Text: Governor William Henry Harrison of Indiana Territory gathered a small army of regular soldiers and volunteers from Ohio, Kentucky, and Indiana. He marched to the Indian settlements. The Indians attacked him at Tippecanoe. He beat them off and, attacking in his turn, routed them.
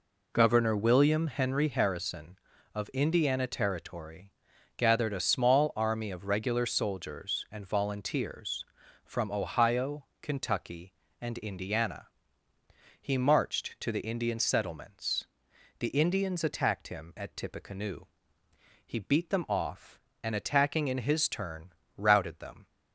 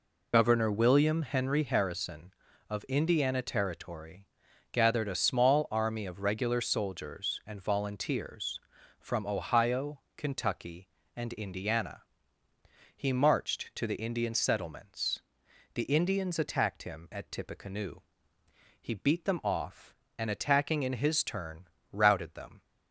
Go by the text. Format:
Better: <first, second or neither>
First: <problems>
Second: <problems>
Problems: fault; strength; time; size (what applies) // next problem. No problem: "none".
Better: first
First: pauses between "Territory" and "gathered"; noticeable; at 4.3 s; 0.46 s long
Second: loses the start of "Governor"; at 0.3 s; 50 ms // pauses between "Territory" and "gathered"; noticeable; at 4.2 s; 0.46 s long